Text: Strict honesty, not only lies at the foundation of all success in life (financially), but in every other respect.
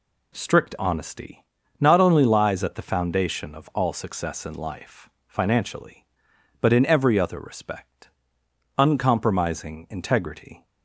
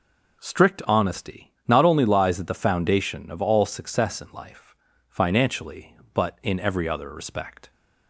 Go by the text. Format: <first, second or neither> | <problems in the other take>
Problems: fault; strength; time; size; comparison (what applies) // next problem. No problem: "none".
second | goes on to say "Uncompromising integrity"; strong; from 8.7 s on; 1.8 s long